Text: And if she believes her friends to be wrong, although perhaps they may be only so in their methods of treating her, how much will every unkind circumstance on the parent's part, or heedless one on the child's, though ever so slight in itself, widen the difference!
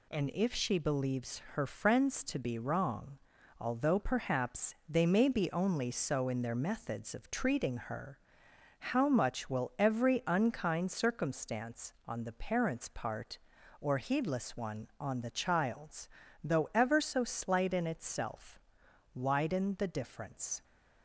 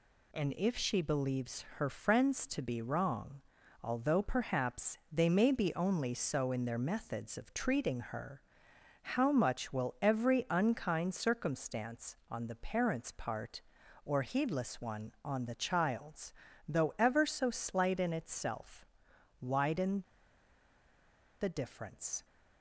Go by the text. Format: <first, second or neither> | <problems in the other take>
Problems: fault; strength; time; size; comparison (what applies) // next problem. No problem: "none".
first | pauses between "widen" and "the"; strong; at 20.0 s; 1.3 s long